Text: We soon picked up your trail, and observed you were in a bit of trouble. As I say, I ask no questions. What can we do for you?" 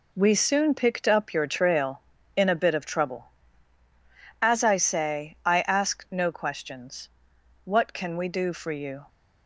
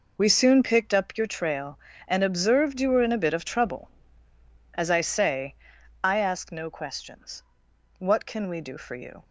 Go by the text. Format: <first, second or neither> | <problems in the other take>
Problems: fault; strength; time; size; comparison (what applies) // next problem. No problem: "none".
second | skips "and observed you were"; at 2.1 s